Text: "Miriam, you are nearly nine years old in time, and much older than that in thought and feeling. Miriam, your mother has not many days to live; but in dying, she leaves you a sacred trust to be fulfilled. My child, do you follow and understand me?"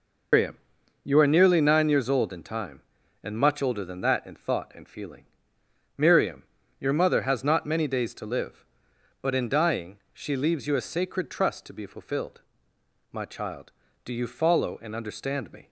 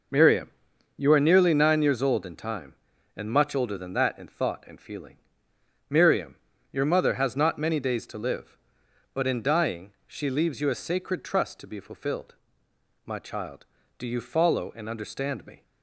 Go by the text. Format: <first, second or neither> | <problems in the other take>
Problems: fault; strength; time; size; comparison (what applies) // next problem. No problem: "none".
second | loses the start of "Miriam"; at 0.3 s; 145 ms